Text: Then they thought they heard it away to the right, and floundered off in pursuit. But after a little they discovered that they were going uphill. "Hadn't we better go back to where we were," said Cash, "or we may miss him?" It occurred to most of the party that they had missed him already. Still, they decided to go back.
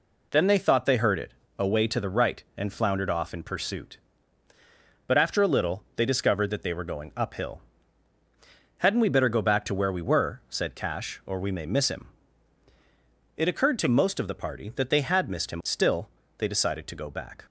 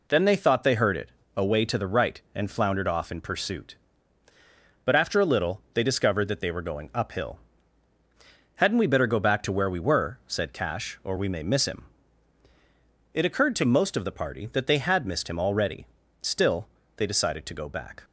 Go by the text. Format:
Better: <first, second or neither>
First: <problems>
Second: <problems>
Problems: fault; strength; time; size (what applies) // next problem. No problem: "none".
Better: second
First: pauses between "it" and "away"; slight; at 1.3 s; 0.26 s long // skips "already"; at 15.6 s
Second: pauses between "it" and "away"; slight; at 1.0 s; 0.26 s long